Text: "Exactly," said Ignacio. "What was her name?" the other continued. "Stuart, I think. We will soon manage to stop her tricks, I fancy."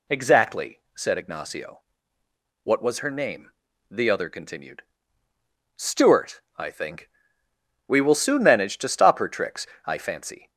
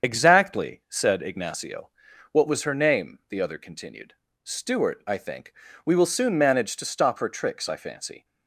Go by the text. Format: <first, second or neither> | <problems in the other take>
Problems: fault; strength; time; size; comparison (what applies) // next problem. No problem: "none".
first | loses the start of "Exactly"; at 0.0 s; 25 ms // starts louder than the rest; strong; until 1.1 s; 7.5 dB